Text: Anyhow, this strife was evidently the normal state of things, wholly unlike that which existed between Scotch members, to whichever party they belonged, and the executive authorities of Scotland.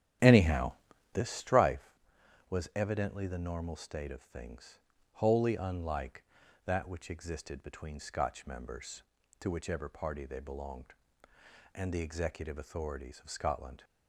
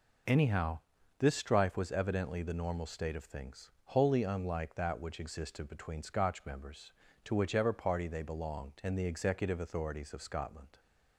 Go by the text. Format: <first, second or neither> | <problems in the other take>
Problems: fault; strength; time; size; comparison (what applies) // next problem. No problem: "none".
second | starts louder than the rest; strong; until 1.9 s; 11 dB